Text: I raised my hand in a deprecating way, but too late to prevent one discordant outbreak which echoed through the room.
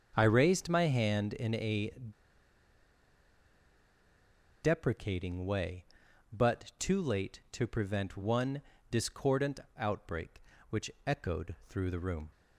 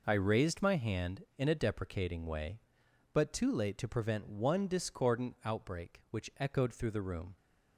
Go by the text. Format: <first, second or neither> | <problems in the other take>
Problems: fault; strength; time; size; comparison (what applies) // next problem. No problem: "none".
second | starts louder than the rest; until 1.1 s; 6.5 dB // pauses between "a" and "deprecating"; strong; at 1.9 s; 2.7 s long // pauses between "one" and "discordant"; slight; at 8.6 s; 0.28 s long // pauses between "discordant" and "outbreak"; slight; at 9.5 s; 0.18 s long // pauses between "which" and "echoed"; slight; at 10.8 s; 0.16 s long